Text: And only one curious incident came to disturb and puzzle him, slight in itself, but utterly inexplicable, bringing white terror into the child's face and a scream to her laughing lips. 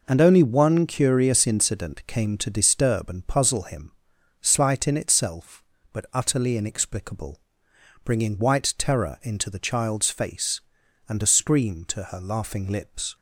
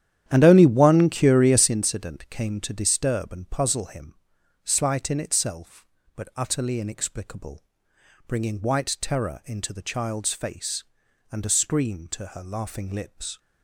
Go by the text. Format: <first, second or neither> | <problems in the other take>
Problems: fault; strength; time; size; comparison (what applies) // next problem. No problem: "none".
first | starts louder than the rest; strong; until 1.7 s; 10.5 dB